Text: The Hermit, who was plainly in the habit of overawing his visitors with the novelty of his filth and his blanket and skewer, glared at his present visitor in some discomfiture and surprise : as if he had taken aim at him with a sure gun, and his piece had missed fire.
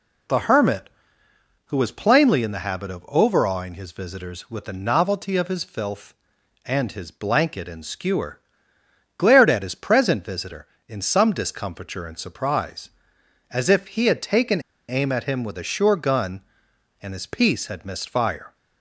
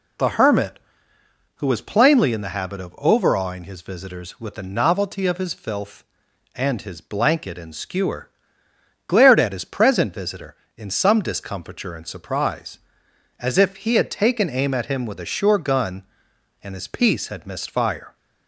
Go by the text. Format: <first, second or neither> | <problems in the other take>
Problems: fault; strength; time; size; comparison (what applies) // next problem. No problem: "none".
second | pauses between "taken" and "aim"; slight; at 14.5 s; 0.28 s long